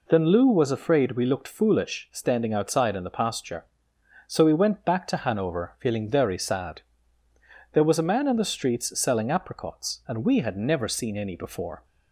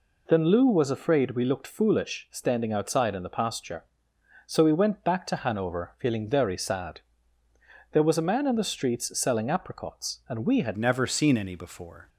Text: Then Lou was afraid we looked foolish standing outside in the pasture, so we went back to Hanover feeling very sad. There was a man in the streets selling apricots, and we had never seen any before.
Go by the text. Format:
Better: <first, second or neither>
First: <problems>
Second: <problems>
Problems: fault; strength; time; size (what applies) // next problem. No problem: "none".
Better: first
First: none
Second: changes voice at "never"; from 10.7 s on; 1.3 s long